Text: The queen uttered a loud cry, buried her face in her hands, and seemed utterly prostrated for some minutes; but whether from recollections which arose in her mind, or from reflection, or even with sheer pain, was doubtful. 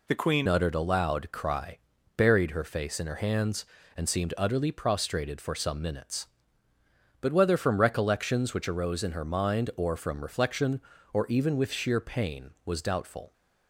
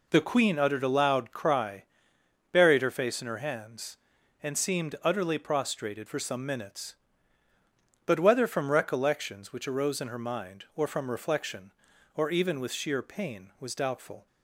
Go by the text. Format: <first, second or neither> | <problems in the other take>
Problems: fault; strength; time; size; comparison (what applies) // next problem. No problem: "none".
second | changes voice at "uttered"; from 0.4 s on; 12.9 s long